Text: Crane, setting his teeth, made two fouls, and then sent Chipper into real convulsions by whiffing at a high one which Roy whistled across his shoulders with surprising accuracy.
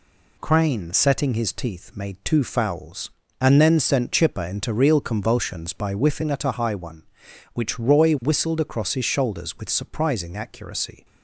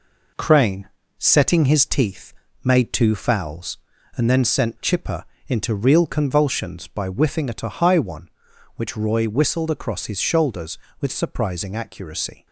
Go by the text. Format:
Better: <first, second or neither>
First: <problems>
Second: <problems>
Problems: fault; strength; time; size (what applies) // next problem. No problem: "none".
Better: first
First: none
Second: gets quieter; noticeable; throughout; 5 dB // pauses between "Chipper" and "into"; slight; at 5.2 s; 0.24 s long